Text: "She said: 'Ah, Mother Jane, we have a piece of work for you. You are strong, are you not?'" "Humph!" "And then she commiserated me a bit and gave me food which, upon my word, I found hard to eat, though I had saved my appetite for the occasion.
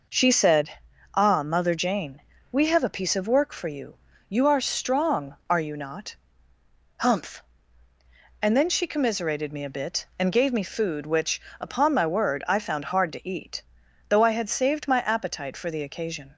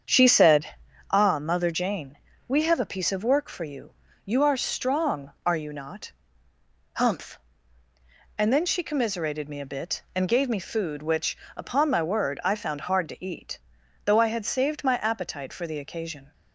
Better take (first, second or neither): first